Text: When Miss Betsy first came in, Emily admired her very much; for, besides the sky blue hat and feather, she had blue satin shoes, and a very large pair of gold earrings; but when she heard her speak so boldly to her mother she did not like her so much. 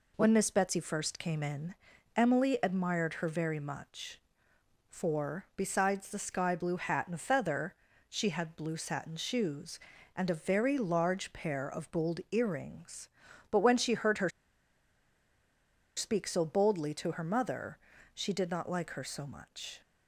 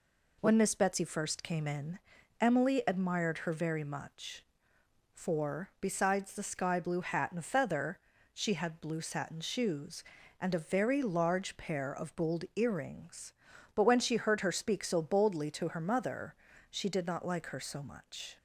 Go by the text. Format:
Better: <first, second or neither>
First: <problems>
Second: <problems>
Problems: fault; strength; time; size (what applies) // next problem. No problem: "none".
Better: second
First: pauses between "her" and "speak"; strong; at 14.2 s; 1.6 s long // pauses between "mother" and "she"; slight; at 17.7 s; 0.34 s long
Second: pauses between "mother" and "she"; slight; at 16.3 s; 0.35 s long